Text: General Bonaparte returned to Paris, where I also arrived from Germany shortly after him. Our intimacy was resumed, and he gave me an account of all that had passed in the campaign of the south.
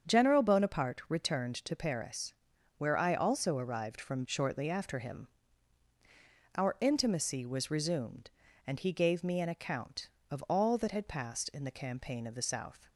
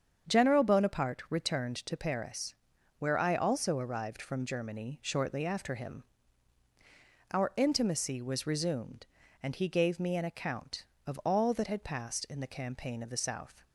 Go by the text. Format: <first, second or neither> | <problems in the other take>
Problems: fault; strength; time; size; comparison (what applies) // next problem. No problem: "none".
second | starts louder than the rest; strong; until 1.1 s; 7.5 dB; strong in the second // skips "Germany"; at 4.2 s